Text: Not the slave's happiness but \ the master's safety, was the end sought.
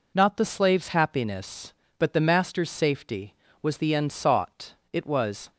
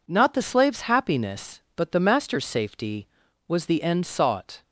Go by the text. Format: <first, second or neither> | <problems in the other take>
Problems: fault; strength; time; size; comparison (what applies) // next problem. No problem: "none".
second | goes on to say "It was"; from 4.9 s on; 0.58 s long